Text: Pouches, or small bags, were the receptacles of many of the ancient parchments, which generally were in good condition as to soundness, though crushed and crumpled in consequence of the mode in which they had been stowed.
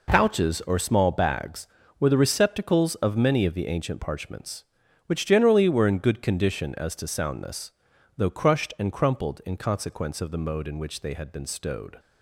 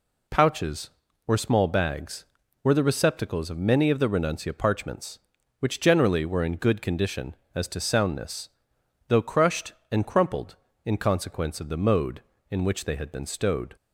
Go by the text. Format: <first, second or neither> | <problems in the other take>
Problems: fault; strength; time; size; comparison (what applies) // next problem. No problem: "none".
first | says "renuncia" for "ancient"; at 4.0 s